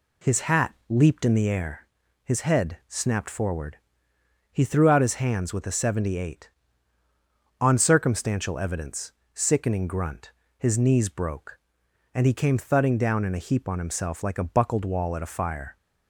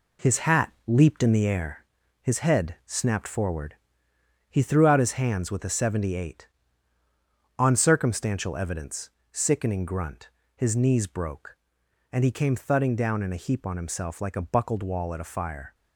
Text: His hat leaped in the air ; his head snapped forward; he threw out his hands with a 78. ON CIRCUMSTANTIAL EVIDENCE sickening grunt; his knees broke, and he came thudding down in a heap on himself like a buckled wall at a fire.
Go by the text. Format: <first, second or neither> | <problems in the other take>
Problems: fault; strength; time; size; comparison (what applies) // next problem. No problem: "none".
first | gets quieter; noticeable; throughout; 5.5 dB // pauses between "hat" and "leaped"; slight; at 0.7 s; 0.16 s long; slight in the first // pauses between "EVIDENCE" and "sickening"; slight; at 9.0 s; 0.24 s long; slight in the first